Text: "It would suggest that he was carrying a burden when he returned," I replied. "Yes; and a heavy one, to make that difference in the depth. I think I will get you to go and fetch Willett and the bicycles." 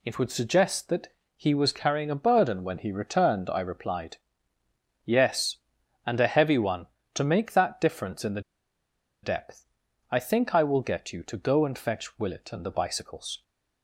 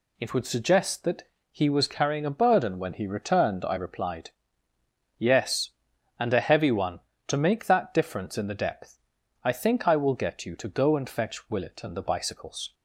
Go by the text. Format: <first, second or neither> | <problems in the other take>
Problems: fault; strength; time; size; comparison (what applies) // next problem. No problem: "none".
second | pauses between "that" and "he"; slight; at 1.1 s; 0.24 s long; slight in the second // pauses between "the" and "depth"; noticeable; at 8.4 s; 0.82 s long